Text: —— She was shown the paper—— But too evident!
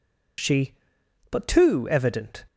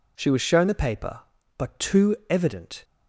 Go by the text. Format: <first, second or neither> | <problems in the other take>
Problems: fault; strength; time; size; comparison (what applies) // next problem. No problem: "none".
second | skips "was shown the paper"; at 1.0 s